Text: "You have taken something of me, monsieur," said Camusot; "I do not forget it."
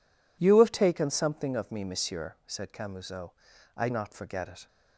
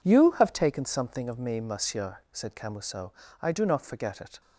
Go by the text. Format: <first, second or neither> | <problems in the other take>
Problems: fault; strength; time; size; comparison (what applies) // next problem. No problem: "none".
second | skips "do"; at 3.8 s